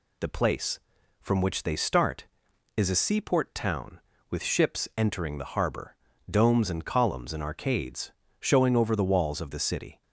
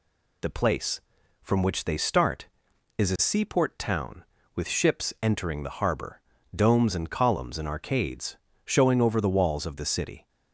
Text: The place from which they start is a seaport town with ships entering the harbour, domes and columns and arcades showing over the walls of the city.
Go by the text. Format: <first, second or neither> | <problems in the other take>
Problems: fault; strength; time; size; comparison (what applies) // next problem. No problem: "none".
neither | pauses between "arcades" and "showing"; slight; the same in both